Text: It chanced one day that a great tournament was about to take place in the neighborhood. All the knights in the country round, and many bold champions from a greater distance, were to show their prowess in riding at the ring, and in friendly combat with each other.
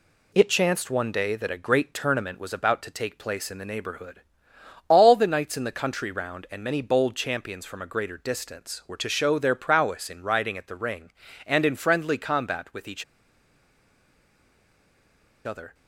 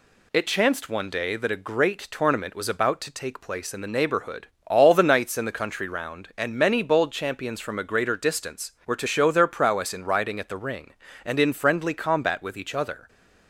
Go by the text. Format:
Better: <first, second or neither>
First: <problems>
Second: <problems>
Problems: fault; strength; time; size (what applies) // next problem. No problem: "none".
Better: second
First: pauses between "each" and "other"; strong; at 13.0 s; 2.4 s long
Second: none